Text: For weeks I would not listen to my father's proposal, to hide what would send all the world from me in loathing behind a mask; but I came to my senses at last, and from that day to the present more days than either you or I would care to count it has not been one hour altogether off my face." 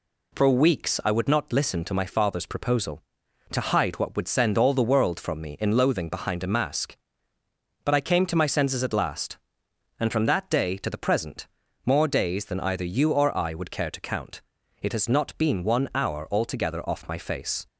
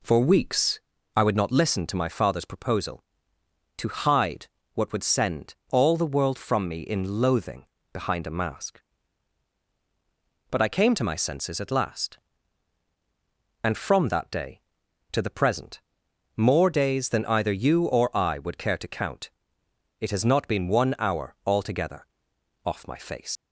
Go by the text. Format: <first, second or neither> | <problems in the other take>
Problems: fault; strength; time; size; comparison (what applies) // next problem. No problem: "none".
first | pauses between "weeks" and "I"; slight; at 0.8 s; 0.34 s long // pauses between "hide" and "what"; slight; at 4.4 s; 0.28 s long // pauses between "send" and "all"; slight; at 5.5 s; 0.16 s long // pauses between "loathing" and "behind"; slight; at 7.6 s; 0.26 s long // pauses between "present" and "more"; noticeable; at 15.8 s; 0.54 s long; slight in the first // pauses between "count" and "it"; noticeable; at 19.3 s; 0.70 s long; also in the first // pauses between "altogether" and "off"; noticeable; at 22.0 s; 0.58 s long // leaves "face" unfinished; at 23.3 s; 115 ms